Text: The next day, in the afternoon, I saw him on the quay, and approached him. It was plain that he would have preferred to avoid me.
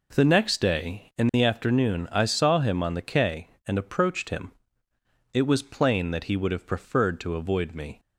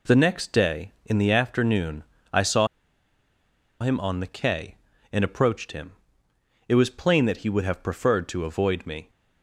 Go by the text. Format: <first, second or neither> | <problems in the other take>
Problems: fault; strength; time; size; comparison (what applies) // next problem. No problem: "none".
first | pauses between "saw" and "him"; at 2.6 s; 1.1 s long